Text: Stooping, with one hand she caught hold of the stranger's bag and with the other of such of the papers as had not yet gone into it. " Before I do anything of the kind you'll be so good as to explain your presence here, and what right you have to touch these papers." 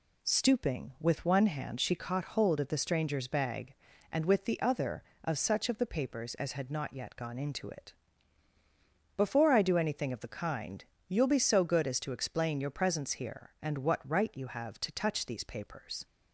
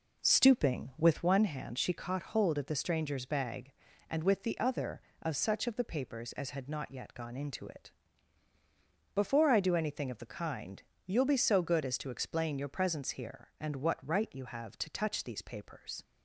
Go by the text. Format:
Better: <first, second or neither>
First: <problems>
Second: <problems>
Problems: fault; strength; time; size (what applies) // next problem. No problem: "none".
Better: first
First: pauses between "kind" and "you'll"; slight; at 10.8 s; 0.22 s long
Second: starts louder than the rest; noticeable; until 1.4 s; 5 dB // pauses between "kind" and "you'll"; slight; at 10.8 s; 0.22 s long